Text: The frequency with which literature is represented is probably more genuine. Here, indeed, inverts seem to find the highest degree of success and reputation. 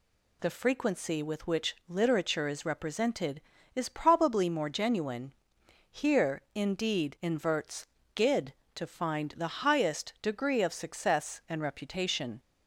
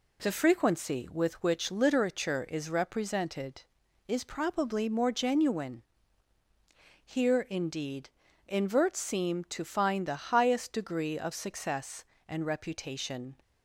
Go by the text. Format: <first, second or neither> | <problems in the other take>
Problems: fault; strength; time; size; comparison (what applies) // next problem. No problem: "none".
second | says "gid" for "seem"; at 8.1 s